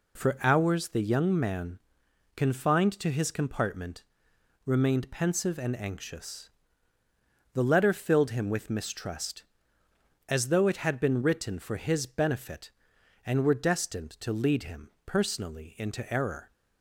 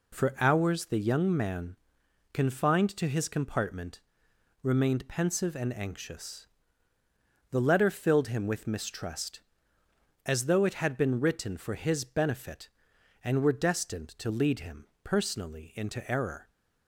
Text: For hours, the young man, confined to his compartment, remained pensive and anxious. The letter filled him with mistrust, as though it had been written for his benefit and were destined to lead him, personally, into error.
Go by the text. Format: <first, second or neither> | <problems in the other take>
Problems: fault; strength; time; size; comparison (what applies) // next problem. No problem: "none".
neither | none